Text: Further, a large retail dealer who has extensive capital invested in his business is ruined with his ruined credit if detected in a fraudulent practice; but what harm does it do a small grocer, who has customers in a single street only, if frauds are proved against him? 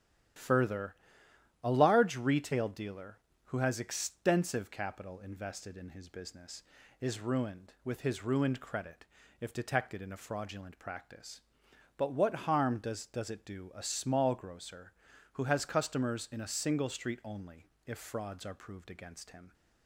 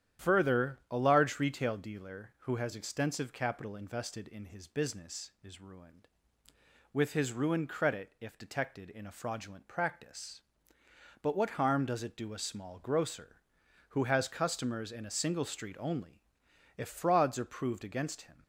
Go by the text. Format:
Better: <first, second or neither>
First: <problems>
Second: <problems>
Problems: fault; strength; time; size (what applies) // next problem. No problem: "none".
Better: second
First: starts louder than the rest; strong; until 2.0 s; 11 dB // pauses between "credit" and "if"; slight; at 9.0 s; 0.36 s long // says "does" twice; at 13.0 s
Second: starts louder than the rest; strong; until 1.3 s; 10 dB